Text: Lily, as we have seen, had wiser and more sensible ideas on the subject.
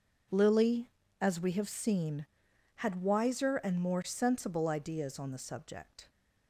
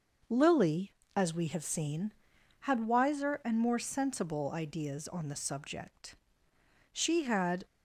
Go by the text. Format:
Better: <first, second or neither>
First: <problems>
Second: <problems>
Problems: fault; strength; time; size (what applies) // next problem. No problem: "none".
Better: first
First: none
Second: goes on to say "She had"; noticeable; from 6.9 s on; 0.72 s long